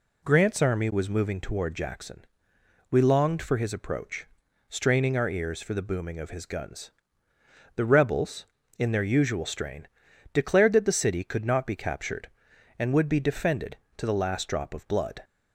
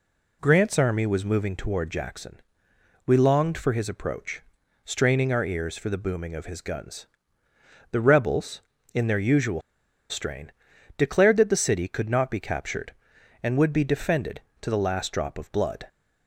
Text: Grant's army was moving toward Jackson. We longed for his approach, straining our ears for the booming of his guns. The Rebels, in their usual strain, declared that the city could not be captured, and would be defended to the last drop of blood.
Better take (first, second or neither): first